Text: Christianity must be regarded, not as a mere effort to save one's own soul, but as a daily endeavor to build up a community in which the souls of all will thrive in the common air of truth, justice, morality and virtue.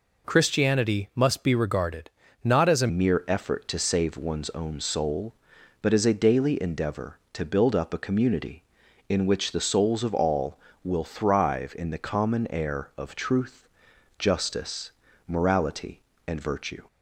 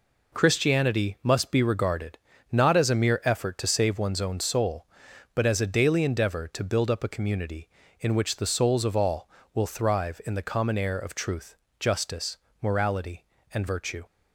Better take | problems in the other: second | changes voice at "mere"; from 2.8 s on; 14.0 s long

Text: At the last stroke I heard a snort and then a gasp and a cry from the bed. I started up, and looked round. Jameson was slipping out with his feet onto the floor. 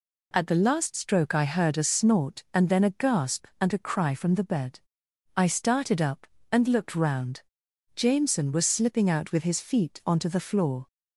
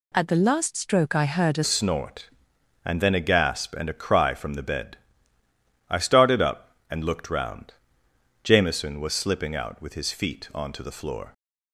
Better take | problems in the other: first | changes voice at "snort"; from 1.6 s on; 9.7 s long

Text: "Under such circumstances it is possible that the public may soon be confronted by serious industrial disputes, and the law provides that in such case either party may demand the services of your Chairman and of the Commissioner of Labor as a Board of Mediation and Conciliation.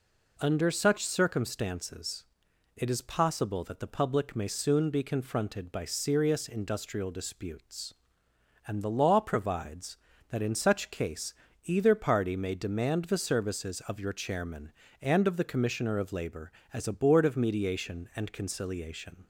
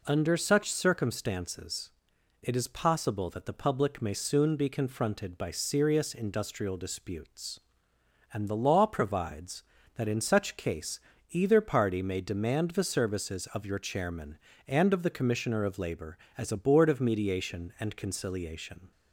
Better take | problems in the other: neither | pauses between "circumstances" and "it"; noticeable; the same in both // pauses between "case" and "either"; slight; the same in both

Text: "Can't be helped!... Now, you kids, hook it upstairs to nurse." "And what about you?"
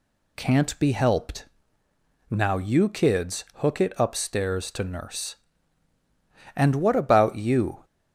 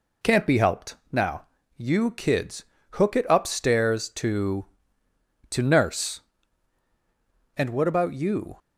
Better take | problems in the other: first | says "to" twice; at 5.5 s

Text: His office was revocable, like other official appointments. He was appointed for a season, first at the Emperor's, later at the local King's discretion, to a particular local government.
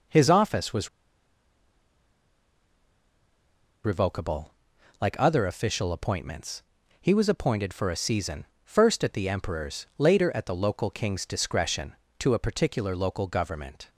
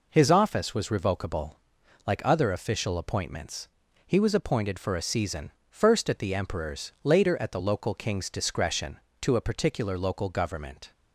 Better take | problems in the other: second | pauses between "was" and "revocable"; strong; at 0.8 s; 2.9 s long

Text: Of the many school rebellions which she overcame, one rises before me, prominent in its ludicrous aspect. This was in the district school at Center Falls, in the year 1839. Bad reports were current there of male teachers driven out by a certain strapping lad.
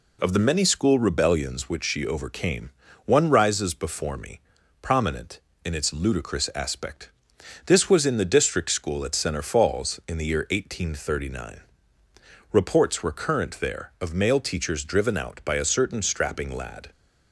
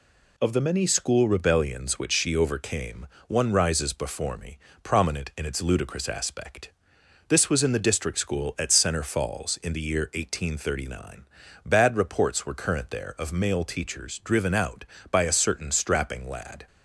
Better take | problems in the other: second | skips "Bad"; at 12.0 s

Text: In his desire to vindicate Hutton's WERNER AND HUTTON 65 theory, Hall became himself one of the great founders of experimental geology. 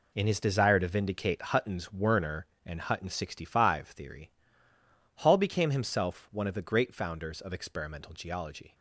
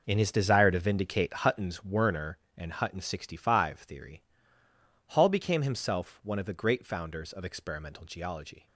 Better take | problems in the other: first | starts louder than the rest; noticeable; until 1.9 s; 5 dB

